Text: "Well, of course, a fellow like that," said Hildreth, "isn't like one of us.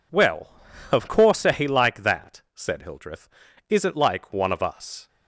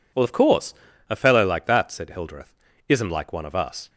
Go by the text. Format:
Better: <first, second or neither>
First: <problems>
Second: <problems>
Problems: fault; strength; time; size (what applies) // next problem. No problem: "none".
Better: second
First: skips "fellow"; at 1.6 s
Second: none